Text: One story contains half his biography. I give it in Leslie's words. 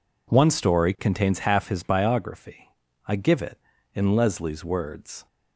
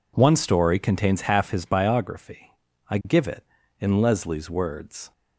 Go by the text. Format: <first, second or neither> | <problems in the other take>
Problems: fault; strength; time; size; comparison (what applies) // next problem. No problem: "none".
neither | none